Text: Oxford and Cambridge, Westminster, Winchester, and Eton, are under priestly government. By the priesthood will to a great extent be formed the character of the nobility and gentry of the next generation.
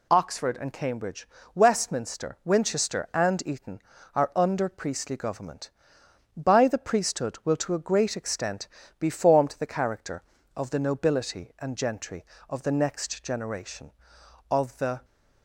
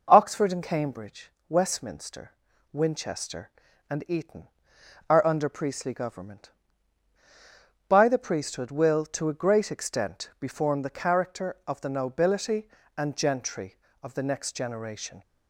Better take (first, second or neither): second